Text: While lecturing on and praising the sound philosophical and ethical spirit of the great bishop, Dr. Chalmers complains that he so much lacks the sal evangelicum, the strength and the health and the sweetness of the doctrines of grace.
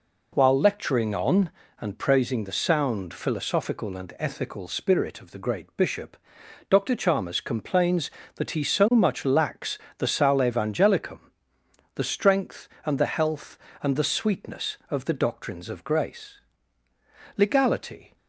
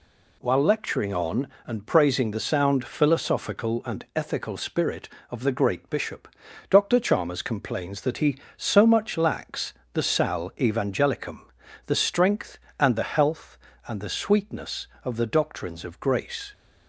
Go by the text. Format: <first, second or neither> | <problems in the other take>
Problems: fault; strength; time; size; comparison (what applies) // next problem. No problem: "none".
second | pauses between "lacks" and "the"; slight; at 9.7 s; 0.18 s long; slight in the second // goes on to say "Legality"; noticeable; from 17.3 s on; 0.78 s long